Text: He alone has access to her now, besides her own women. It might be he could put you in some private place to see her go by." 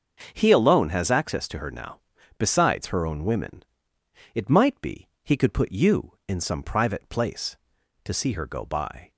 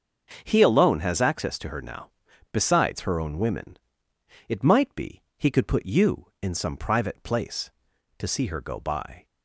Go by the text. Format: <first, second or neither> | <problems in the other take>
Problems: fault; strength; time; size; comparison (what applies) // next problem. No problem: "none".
neither | starts louder than the rest; the same in both